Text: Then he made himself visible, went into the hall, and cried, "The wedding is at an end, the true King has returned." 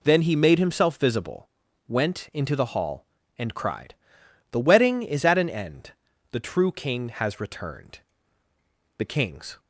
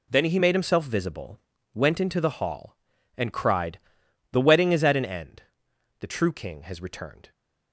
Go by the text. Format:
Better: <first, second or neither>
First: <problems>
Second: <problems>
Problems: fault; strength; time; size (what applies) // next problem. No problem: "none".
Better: second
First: goes on to say "The kings"; noticeable; from 8.9 s on; 0.62 s long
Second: none